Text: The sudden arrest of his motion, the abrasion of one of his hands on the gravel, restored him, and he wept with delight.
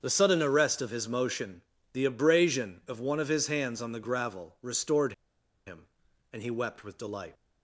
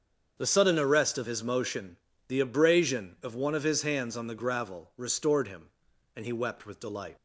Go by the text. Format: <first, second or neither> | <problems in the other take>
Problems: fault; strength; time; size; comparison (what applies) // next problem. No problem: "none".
second | starts louder than the rest; strong; until 1.0 s; 7 dB; strong in the second // pauses between "restored" and "him"; noticeable; at 5.1 s; 0.54 s long